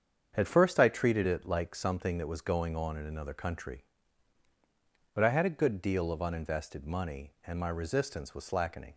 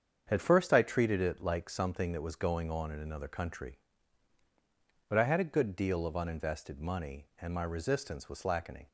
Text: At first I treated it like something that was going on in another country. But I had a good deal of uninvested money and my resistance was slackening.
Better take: neither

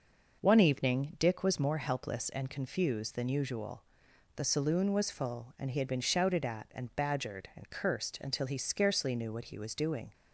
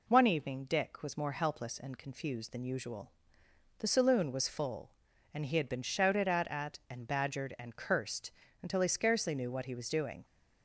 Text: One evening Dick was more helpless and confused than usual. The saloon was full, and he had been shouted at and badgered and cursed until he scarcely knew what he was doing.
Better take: first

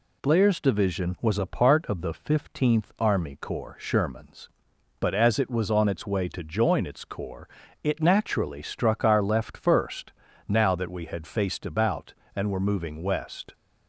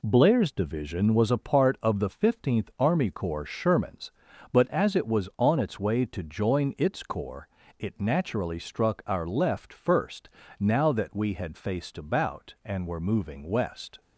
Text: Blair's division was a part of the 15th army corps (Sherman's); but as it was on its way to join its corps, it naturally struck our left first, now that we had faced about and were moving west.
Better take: neither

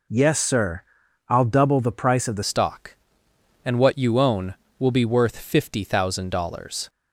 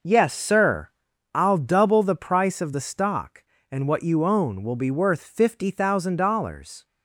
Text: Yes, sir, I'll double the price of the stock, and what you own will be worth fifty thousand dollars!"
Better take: second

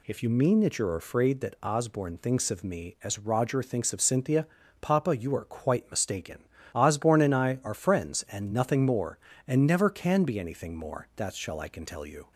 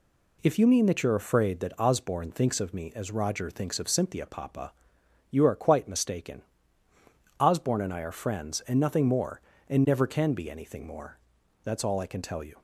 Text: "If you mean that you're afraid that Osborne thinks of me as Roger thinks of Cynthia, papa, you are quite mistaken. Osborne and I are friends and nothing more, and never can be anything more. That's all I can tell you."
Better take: second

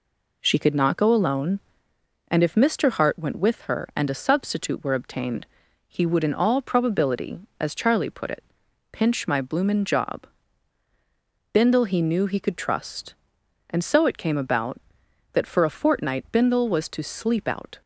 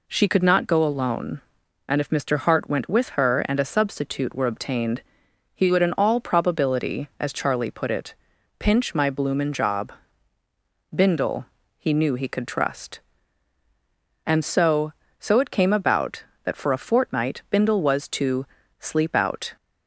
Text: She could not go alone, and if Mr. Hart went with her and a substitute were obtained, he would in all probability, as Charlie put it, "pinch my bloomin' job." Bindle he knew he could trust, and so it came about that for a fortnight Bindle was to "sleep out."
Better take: first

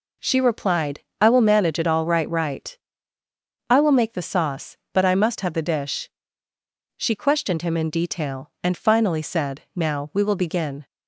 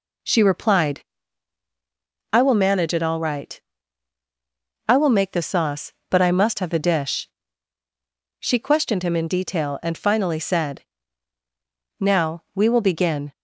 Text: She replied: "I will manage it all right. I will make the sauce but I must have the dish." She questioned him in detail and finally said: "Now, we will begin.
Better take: second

